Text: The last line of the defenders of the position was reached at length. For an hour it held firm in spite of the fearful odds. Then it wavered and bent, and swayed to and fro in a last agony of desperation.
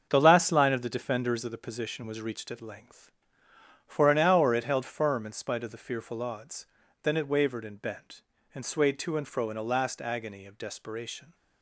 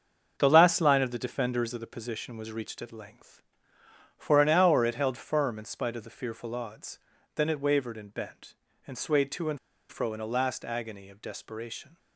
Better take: first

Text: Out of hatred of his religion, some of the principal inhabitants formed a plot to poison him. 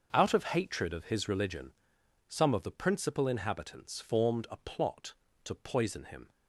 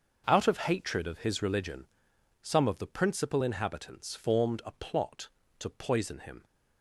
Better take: neither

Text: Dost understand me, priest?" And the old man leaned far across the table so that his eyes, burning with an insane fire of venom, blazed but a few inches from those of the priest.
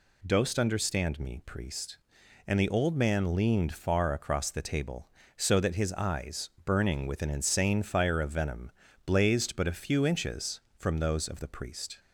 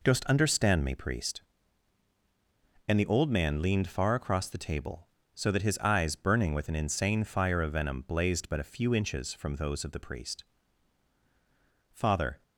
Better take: first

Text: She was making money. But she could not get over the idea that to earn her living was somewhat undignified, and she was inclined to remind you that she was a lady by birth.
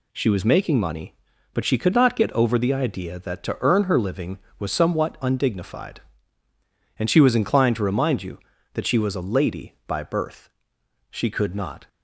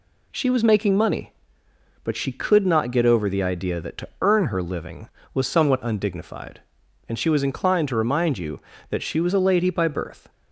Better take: second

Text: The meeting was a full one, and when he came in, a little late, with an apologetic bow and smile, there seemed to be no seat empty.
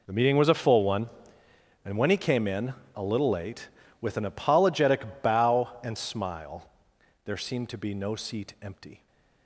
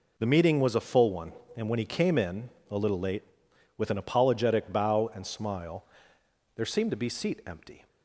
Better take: first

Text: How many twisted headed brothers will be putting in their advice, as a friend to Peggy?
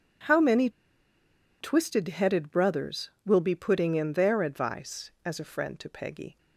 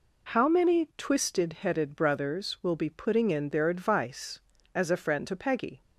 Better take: second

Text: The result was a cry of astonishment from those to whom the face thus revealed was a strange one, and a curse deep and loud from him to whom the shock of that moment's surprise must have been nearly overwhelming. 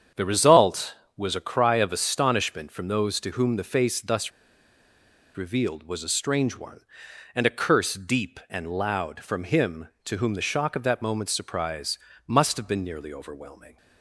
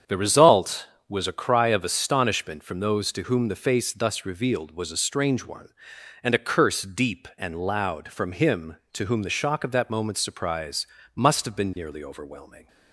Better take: second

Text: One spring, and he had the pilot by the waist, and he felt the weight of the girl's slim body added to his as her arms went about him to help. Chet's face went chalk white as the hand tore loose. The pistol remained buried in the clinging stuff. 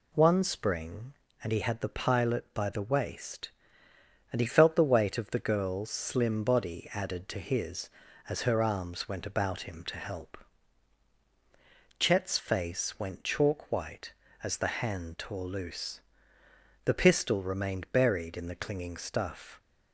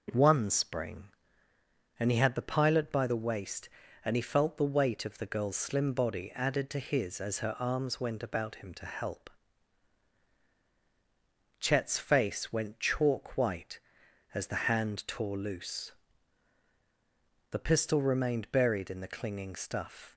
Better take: neither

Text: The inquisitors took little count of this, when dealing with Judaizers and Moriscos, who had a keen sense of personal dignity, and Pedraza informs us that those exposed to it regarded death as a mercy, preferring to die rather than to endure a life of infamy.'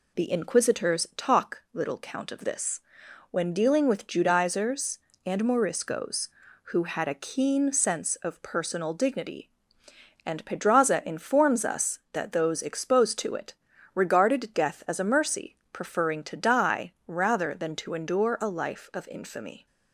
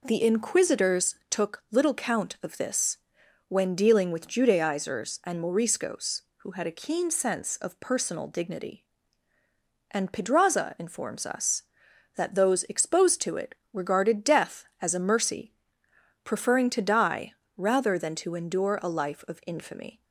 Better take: second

